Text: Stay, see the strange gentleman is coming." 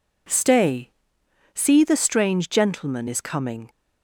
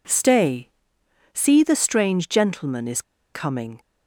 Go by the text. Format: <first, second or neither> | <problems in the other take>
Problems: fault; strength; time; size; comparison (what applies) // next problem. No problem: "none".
first | pauses between "is" and "coming"; slight; at 3.0 s; 0.31 s long